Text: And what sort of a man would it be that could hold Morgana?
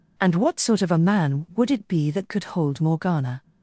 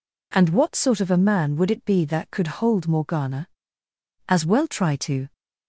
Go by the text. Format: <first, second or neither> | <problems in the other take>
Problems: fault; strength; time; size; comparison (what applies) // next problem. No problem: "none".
first | goes on to say "As well try to"; noticeable; from 4.2 s on; 1.0 s long